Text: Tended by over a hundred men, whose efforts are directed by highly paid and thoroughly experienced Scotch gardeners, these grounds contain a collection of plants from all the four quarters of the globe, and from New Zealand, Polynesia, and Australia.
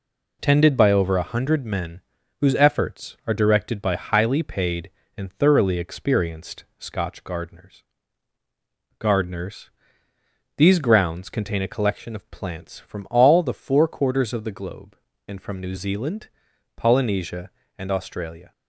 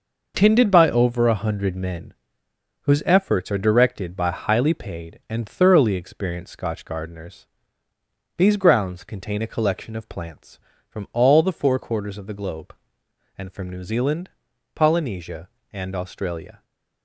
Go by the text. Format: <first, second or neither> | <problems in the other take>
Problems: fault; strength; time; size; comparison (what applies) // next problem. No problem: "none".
second | says "gardeners" twice; at 8.9 s